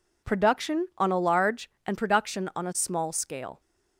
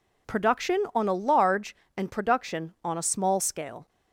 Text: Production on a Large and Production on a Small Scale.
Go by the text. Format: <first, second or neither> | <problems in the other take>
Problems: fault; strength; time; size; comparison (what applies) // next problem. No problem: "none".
neither | none